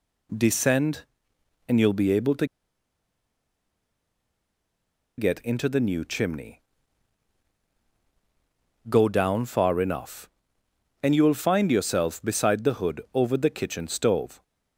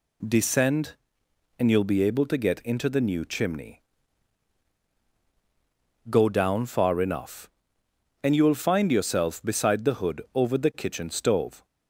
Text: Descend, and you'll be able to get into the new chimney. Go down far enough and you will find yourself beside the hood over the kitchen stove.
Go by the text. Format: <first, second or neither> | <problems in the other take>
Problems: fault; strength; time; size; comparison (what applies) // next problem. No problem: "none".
second | pauses between "to" and "get"; strong; at 2.4 s; 2.7 s long